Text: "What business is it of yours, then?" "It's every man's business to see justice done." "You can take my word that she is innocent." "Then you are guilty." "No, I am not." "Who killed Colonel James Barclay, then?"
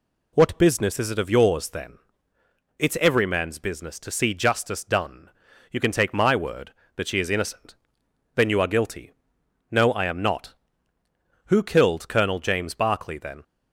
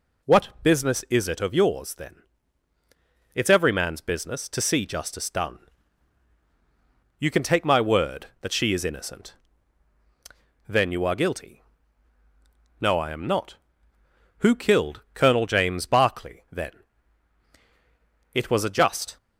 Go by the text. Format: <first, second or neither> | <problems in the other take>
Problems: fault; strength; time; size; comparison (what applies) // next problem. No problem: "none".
first | goes on to say "It was a just"; noticeable; from 18.3 s on; 0.84 s long